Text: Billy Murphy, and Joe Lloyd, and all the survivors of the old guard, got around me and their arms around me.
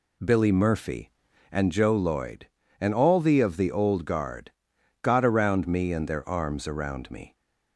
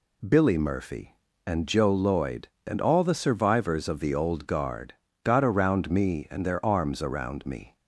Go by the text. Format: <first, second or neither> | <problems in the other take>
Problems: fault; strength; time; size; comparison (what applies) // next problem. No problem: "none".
second | skips "survivors"; at 3.4 s